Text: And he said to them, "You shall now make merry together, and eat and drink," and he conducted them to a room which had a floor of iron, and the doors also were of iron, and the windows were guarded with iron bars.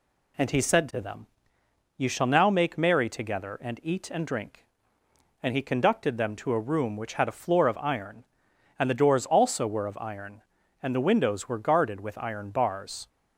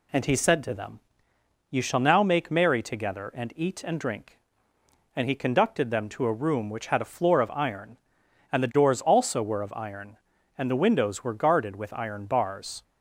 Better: neither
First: none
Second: none

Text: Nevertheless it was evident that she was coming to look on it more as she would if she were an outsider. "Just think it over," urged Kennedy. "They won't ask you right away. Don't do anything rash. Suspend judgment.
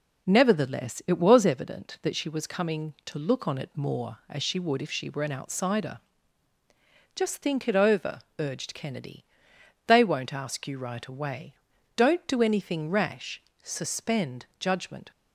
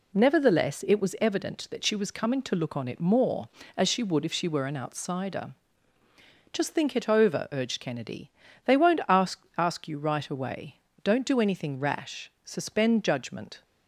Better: first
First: none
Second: says "ask" twice; at 9.5 s

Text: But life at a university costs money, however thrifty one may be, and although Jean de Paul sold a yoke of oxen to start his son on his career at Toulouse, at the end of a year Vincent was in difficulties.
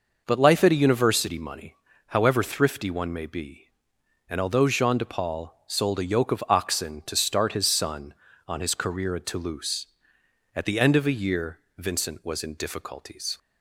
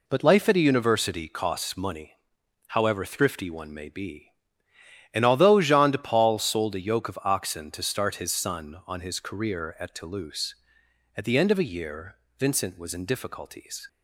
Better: second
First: skips "costs"; at 1.3 s // pauses between "year" and "Vincent"; slight; at 11.5 s; 0.18 s long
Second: pauses between "year" and "Vincent"; slight; at 12.1 s; 0.20 s long

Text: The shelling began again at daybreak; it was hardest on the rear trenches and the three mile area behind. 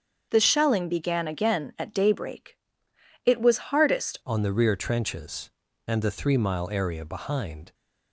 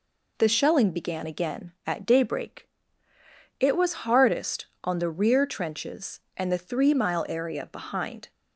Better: second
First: starts louder than the rest; until 1.3 s; 7 dB // changes voice at "on"; from 4.2 s on; 3.5 s long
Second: none

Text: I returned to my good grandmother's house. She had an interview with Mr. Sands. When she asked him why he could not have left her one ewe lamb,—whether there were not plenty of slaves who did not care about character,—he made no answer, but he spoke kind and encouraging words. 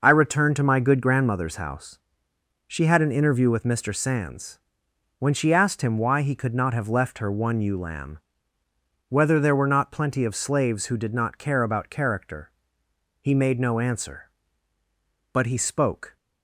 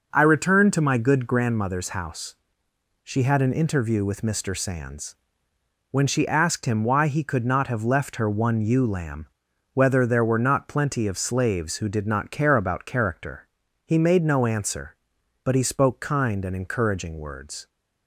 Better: second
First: stops before "kind and encouraging words"; at 16.1 s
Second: none

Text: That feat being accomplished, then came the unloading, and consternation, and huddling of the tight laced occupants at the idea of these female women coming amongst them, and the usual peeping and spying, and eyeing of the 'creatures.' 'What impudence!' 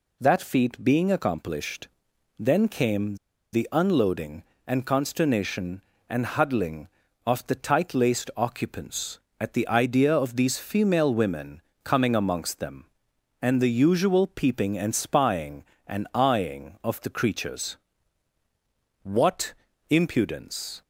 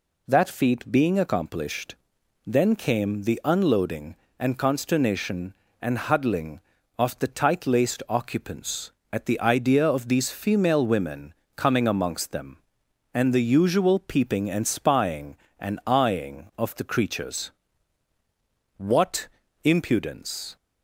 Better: second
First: pauses between "came" and "the"; at 3.1 s; 0.36 s long // pauses between "women" and "coming"; slight; at 11.6 s; 0.22 s long // pauses between "What" and "impudence"; slight; at 19.5 s; 0.36 s long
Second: pauses between "women" and "coming"; slight; at 11.3 s; 0.22 s long // pauses between "What" and "impudence"; slight; at 19.2 s; 0.36 s long

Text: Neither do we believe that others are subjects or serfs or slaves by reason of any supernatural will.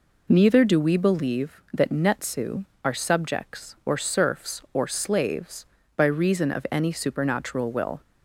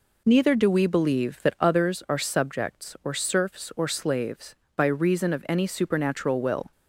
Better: second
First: says "netsu" for "others"; at 1.8 s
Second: none

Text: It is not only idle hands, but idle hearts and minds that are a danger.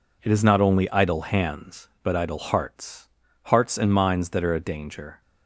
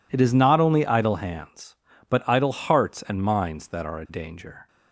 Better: second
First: says "hearts" twice; at 3.4 s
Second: none

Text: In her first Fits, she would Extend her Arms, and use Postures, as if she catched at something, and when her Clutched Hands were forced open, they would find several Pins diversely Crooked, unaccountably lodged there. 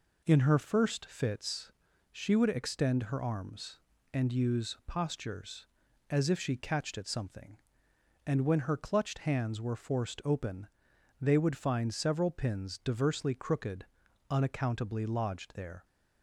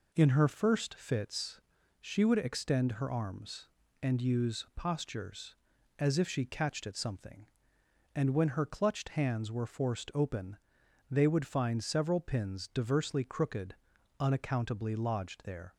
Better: neither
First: none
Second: none

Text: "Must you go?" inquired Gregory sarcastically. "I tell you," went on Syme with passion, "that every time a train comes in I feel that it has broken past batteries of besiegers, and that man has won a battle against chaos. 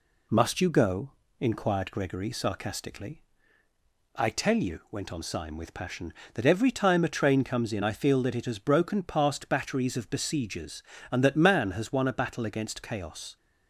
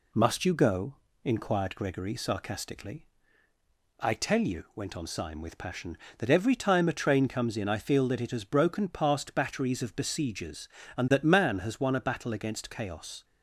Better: neither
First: none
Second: none

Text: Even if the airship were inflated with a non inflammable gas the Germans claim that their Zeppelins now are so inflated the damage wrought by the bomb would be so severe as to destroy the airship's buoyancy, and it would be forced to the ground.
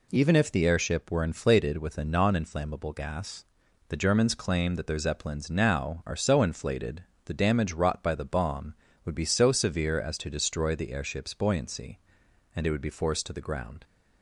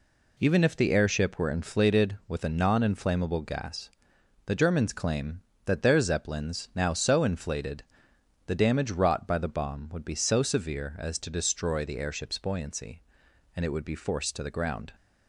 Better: first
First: pauses between "gas" and "the"; noticeable; at 3.4 s; 0.46 s long // pauses between "inflated" and "the"; slight; at 7.0 s; 0.22 s long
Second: pauses between "gas" and "the"; noticeable; at 3.8 s; 0.56 s long // skips "are"; at 6.9 s // pauses between "inflated" and "the"; noticeable; at 7.8 s; 0.62 s long

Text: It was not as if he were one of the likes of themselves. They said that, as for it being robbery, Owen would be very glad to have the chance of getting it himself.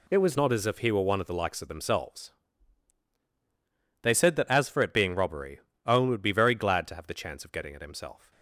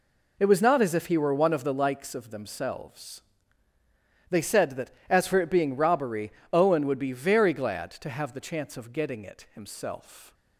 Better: second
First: changes voice at "not"; from 0.3 s on; 8.0 s long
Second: none

